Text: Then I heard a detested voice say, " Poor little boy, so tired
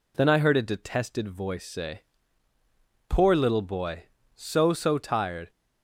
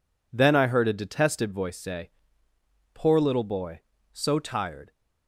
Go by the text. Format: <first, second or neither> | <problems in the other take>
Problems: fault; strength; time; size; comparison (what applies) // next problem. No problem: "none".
second | says "so" twice; at 4.7 s